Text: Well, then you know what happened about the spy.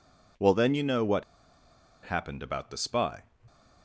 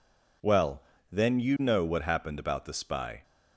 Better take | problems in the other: second | pauses between "what" and "happened"; noticeable; at 1.2 s; 0.80 s long

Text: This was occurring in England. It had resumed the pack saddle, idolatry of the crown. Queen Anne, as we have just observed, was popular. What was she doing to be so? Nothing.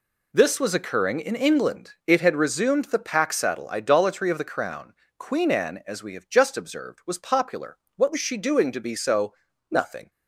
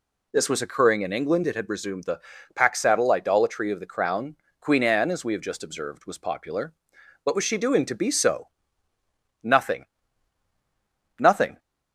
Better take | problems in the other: first | pauses between "the" and "pack"; slight; at 2.2 s; 0.34 s long // says "Nothing" twice; at 11.1 s

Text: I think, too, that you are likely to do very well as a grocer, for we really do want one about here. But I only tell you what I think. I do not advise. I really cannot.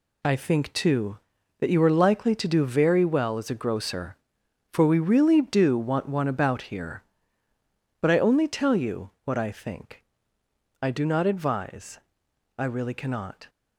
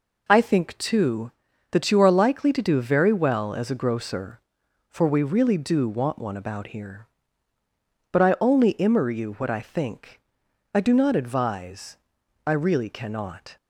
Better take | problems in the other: first | says "immer" for "tell"; at 8.7 s

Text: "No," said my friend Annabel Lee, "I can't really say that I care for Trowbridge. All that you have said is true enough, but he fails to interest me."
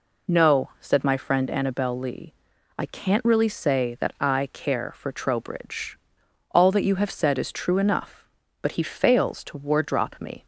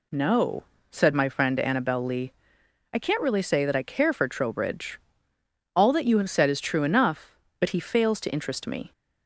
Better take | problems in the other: second | says "wardrop" for "interest"; at 9.5 s

